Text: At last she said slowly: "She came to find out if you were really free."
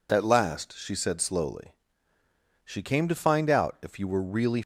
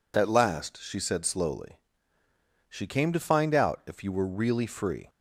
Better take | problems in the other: second | stops before "free"; at 4.6 s

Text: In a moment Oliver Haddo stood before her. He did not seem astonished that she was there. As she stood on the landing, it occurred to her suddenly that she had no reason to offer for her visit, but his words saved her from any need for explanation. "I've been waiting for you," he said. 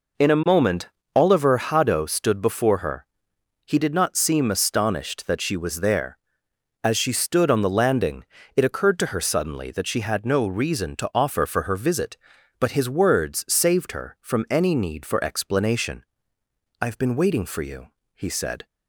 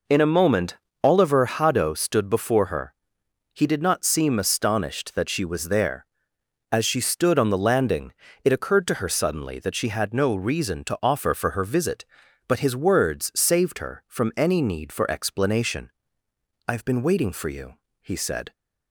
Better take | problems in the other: neither | pauses between "moment" and "Oliver"; slight; the same in both

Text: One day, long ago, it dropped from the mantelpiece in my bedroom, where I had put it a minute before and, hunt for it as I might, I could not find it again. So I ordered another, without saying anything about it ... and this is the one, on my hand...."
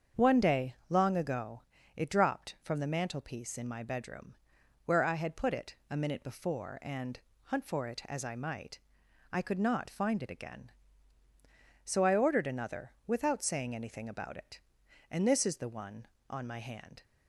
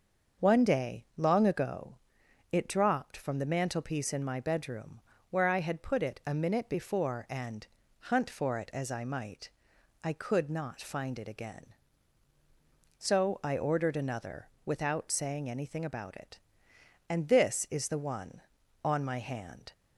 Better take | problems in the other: neither | starts louder than the rest; the same in both

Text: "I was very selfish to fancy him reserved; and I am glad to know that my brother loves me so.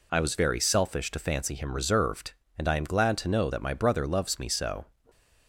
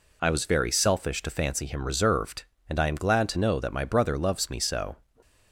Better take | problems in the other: neither | none

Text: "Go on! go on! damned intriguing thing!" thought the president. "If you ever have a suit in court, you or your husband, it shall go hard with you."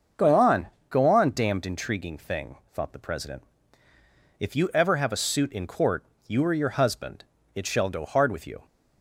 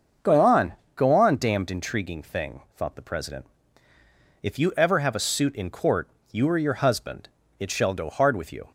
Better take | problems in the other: neither | starts louder than the rest; the same in both

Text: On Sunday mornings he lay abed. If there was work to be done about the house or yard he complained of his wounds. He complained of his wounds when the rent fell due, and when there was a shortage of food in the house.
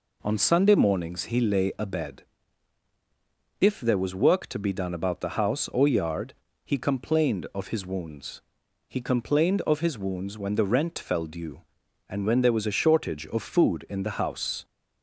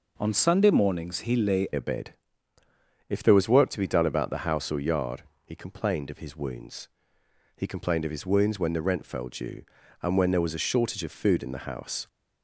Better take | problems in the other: first | changes voice at "abed"; from 1.7 s on; 10.3 s long // pauses between "yard" and "he"; slight; at 5.2 s; 0.22 s long; slight in the first

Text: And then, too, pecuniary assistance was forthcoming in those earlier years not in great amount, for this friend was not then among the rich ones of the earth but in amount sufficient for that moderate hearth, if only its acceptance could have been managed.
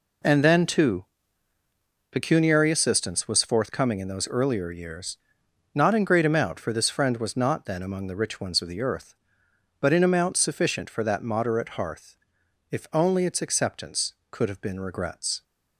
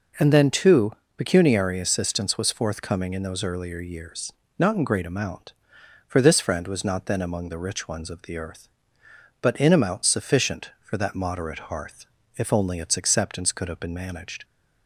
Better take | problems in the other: second | pauses between "years" and "not"; noticeable; at 5.1 s; 0.58 s long; slight in the second // says "regrets" for "managed"; at 14.7 s

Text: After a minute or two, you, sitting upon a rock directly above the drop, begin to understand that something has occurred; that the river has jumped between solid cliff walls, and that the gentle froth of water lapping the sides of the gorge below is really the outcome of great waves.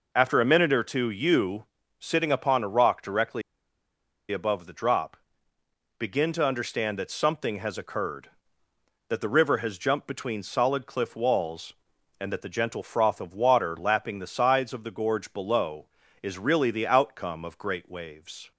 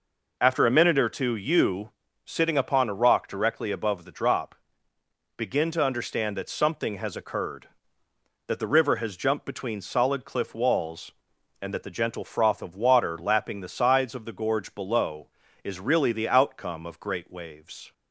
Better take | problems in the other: second | pauses between "directly" and "above"; noticeable; at 3.4 s; 0.89 s long

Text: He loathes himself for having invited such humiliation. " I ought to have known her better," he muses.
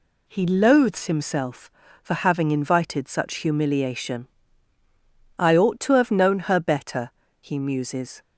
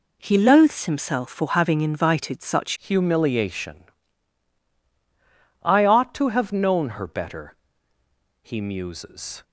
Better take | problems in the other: first | changes voice at "humiliation"; from 2.7 s on; 6.7 s long

